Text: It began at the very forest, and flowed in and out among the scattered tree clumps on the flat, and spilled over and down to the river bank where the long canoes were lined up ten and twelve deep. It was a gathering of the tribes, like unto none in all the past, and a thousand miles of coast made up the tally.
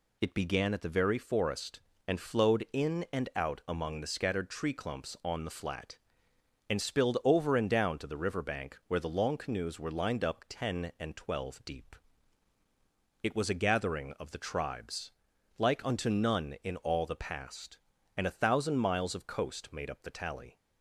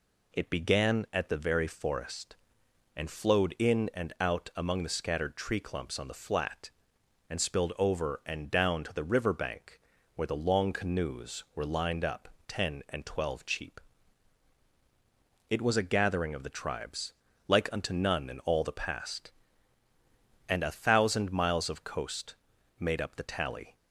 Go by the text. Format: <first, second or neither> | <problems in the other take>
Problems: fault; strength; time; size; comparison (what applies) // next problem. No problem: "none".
first | pauses between "bank" and "where"; slight; at 9.7 s; 0.36 s long // pauses between "up" and "ten"; slight; at 12.2 s; 0.18 s long // says "cheap" for "deep"; at 13.4 s // pauses between "coast" and "made"; at 22.3 s; 0.44 s long